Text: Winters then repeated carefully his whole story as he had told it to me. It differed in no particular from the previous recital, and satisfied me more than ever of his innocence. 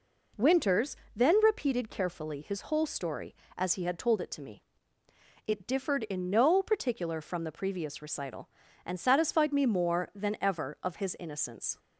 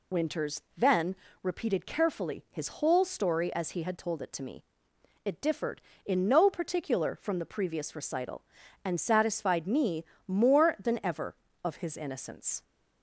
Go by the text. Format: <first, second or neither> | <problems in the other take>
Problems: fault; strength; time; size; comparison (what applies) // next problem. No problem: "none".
first | loses the start of "Winters"; at 0.1 s; 45 ms // pauses between "Winters" and "then"; slight; at 0.6 s; 0.16 s long; slight in the first // pauses between "then" and "repeated"; slight; at 1.1 s; 0.26 s long // pauses between "me" and "more"; slight; at 10.0 s; 0.24 s long